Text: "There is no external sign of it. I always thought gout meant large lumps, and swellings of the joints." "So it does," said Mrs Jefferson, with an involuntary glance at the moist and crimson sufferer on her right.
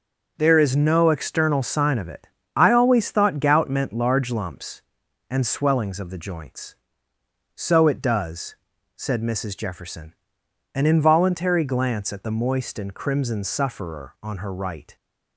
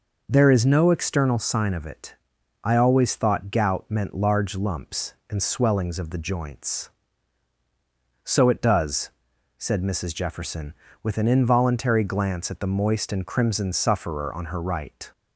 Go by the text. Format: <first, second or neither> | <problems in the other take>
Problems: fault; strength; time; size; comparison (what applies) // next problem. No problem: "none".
second | starts louder than the rest; noticeable; until 1.3 s; 6 dB // skips "with"; at 10.4 s